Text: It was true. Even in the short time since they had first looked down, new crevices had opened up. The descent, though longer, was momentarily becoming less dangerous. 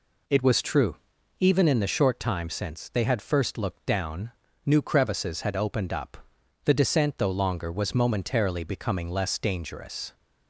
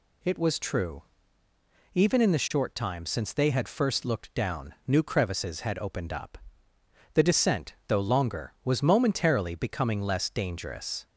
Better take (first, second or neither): neither